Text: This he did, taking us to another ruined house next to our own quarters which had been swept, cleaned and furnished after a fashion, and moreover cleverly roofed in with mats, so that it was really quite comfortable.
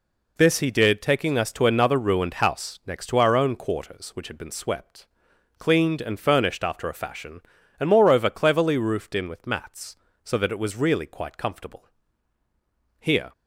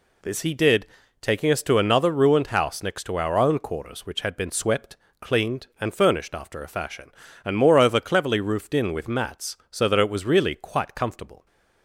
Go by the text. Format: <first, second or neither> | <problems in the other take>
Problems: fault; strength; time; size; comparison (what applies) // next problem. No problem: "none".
second | goes on to say "Here"; slight; from 12.9 s on; 0.32 s long